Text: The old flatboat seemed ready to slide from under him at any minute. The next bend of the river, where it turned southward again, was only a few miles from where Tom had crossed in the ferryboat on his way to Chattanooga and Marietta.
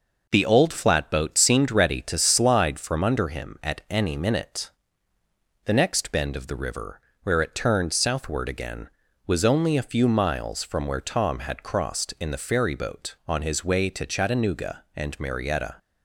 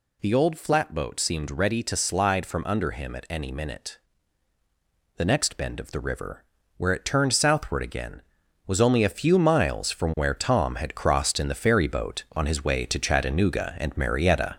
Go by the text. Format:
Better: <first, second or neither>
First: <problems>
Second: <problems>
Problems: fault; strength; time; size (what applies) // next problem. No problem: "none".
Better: first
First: none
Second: gets louder; noticeable; throughout; 4 dB